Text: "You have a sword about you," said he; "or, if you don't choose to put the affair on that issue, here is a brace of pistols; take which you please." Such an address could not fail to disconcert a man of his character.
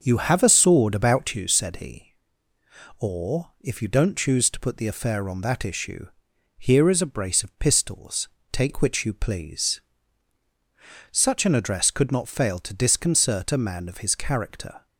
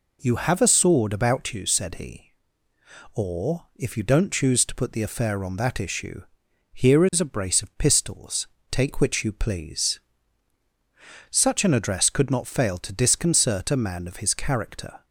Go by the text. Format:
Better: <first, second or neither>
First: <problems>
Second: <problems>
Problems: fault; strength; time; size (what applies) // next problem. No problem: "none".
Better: second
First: starts louder than the rest; until 1.7 s; 6 dB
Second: none